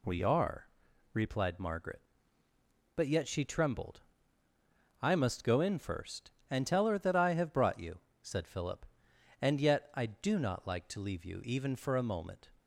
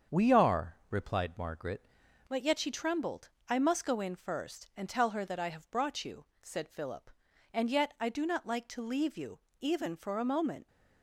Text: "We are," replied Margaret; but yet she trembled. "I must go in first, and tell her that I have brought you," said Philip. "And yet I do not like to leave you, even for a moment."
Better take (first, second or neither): first